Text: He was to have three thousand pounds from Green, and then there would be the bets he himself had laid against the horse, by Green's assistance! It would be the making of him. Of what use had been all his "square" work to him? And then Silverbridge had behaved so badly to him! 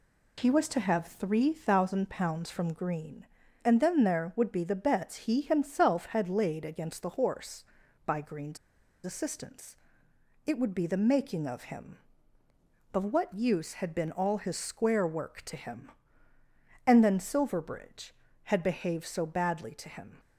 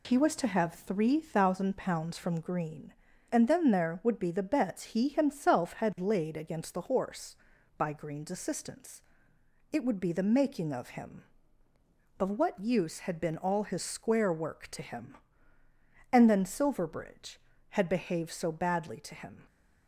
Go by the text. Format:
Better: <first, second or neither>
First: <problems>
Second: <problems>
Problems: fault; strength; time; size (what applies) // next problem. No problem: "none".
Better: second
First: pauses between "Green's" and "assistance"; noticeable; at 8.5 s; 0.48 s long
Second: none